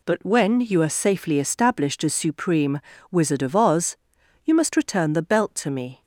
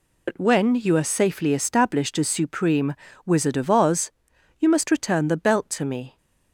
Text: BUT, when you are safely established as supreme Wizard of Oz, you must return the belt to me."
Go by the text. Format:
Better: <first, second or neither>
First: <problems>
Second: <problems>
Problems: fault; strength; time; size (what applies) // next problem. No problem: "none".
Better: first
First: pauses between "supreme" and "Wizard"; slight; at 2.8 s; 0.32 s long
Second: loses the start of "BUT"; at 0.2 s; 85 ms // pauses between "supreme" and "Wizard"; slight; at 2.9 s; 0.32 s long